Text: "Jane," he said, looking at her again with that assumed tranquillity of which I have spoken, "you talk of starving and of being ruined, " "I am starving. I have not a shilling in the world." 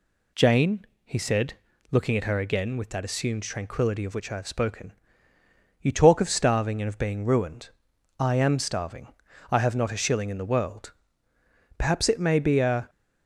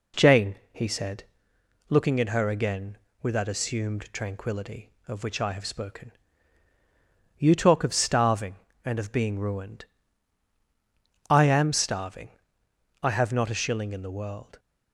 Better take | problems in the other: second | goes on to say "Perhaps it may be a"; noticeable; from 11.7 s on; 1.1 s long

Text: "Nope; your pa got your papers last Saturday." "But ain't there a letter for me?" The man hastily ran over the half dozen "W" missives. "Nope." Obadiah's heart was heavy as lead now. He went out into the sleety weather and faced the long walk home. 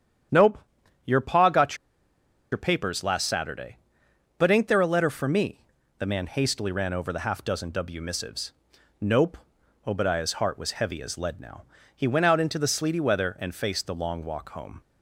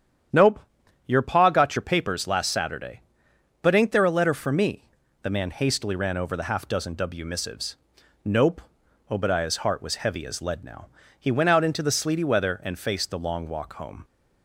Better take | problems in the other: second | starts louder than the rest; strong; until 2.5 s; 9.5 dB; strong in the second // pauses between "got" and "your"; noticeable; at 1.7 s; 0.76 s long

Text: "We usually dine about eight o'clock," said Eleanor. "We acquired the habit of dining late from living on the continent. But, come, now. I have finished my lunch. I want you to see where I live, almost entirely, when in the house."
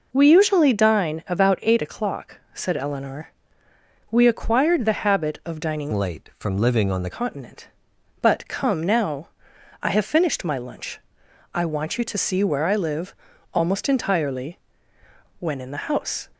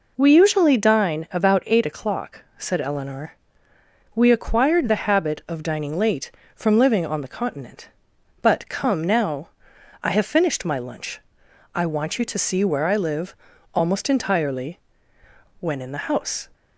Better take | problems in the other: second | changes voice from "late" to "the"; from 5.9 to 7.0 s; 1.1 s long

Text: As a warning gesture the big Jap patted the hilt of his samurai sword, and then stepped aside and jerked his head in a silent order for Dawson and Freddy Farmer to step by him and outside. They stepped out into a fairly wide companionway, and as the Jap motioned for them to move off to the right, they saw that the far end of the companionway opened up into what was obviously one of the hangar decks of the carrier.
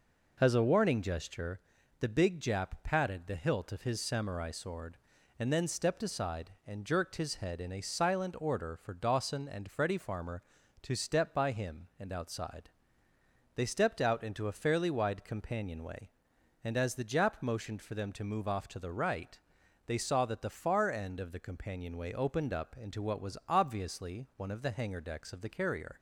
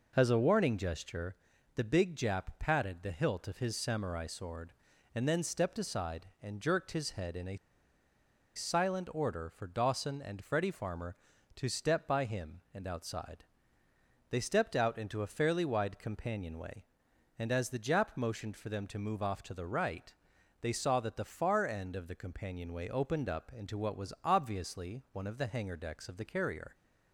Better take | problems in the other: first | pauses between "gesture" and "the"; at 1.3 s; 0.40 s long; also in the first // pauses between "a" and "silent"; at 7.5 s; 0.99 s long

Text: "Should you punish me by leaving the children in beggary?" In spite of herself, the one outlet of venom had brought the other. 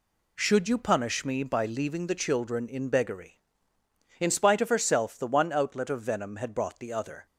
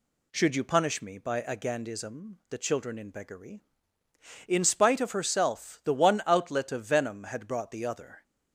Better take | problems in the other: first | says "agandism" for "leaving"; at 1.4 s

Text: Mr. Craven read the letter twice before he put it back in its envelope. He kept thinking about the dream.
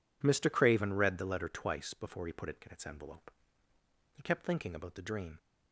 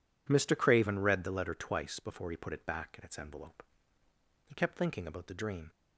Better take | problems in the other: second | skips "back"; at 2.6 s

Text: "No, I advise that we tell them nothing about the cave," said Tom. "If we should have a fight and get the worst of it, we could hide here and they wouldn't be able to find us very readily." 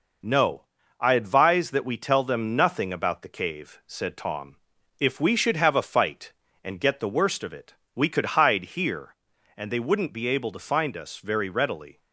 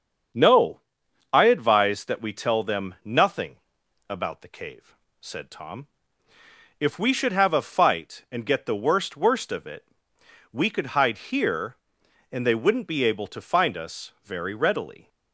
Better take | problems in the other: first | starts louder than the rest; strong; until 1.8 s; 7 dB // pauses between "nothing" and "about"; noticeable; at 3.5 s; 0.52 s long // says "worst" twice; at 9.1 s

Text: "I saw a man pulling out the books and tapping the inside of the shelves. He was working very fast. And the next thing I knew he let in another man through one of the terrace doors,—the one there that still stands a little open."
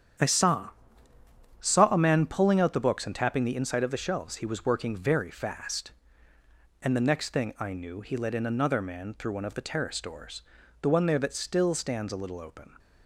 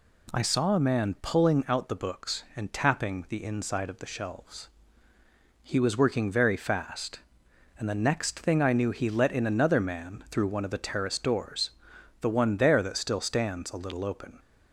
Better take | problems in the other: second | starts louder than the rest; strong; until 2.1 s; 9 dB // says "saw" twice; at 1.6 s

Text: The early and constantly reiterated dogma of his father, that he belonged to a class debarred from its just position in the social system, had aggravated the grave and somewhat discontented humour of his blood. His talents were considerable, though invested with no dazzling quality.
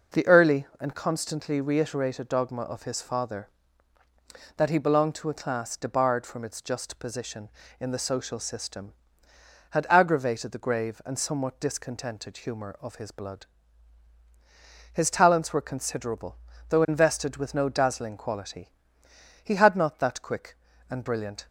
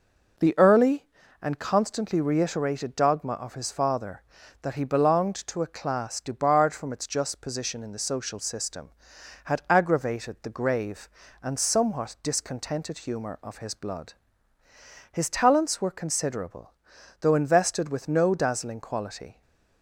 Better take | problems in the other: second | goes on to say "He had not that quick and brilliant"; strong; from 19.4 s on; 2.0 s long

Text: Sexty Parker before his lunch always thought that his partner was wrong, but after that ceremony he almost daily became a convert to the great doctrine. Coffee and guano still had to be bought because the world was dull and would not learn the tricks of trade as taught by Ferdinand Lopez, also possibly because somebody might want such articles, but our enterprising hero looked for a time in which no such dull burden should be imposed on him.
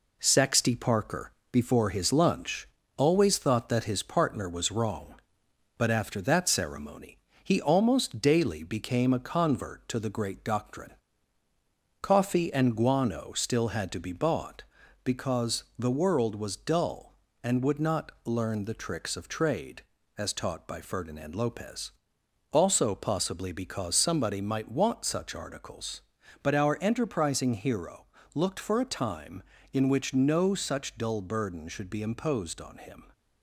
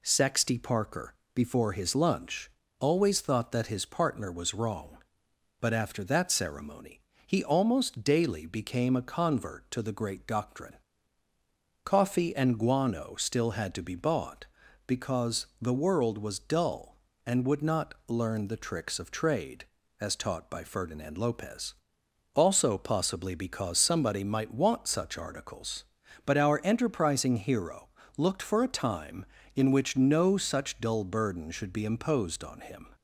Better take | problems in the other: second | gets quieter; throughout; 4 dB // pauses between "Parker" and "before"; slight; at 1.3 s; 0.22 s long; slight in the second // pauses between "lunch" and "always"; slight; at 2.6 s; 0.30 s long; slight in the second // pauses between "ceremony" and "he"; slight; at 7.1 s; 0.24 s long; slight in the second // pauses between "because" and "the"; slight; at 15.6 s; 0.16 s long; slight in the second // pauses between "hero" and "looked"; slight; at 28.0 s; 0.30 s long; slight in the second

